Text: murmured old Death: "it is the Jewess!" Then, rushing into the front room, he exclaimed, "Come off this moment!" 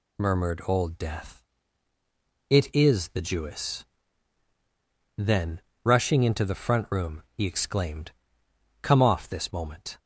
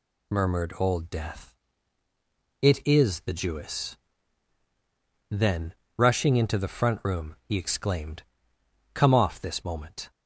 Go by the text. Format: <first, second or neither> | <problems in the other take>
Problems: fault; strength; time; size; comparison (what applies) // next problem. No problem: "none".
neither | none